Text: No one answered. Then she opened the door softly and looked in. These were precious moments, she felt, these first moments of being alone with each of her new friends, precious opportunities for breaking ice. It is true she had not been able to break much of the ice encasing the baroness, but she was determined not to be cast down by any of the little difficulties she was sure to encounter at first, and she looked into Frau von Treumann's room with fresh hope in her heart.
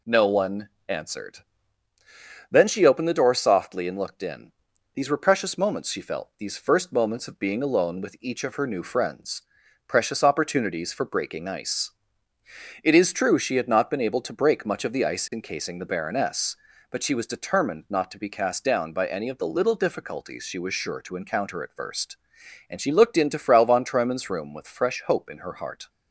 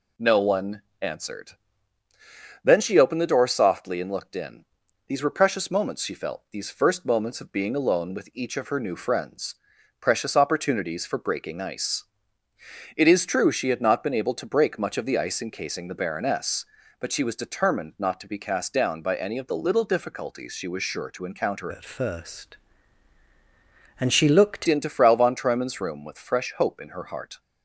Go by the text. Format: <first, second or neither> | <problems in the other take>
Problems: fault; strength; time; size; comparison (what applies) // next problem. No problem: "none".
first | pauses between "one" and "answered"; slight; at 0.8 s; 0.22 s long; slight in the first // changes voice from "at" to "looked"; from 21.6 to 24.6 s; 3.0 s long